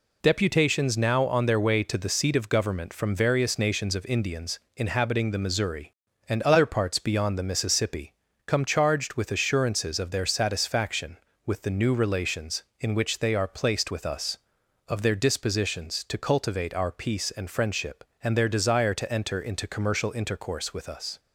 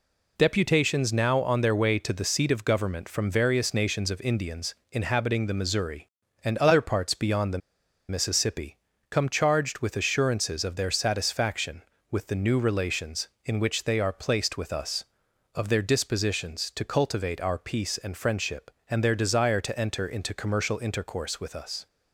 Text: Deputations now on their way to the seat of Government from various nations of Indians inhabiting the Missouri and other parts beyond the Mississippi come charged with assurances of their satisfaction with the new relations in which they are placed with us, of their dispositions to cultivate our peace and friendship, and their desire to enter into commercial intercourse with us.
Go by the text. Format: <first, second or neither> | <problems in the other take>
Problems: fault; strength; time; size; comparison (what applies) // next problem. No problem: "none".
first | pauses between "Indians" and "inhabiting"; slight; at 4.7 s; 0.18 s long; slight in the first // pauses between "the" and "Mississippi"; noticeable; at 7.5 s; 0.50 s long // pauses between "Mississippi" and "come"; slight; at 8.7 s; 0.32 s long; slight in the first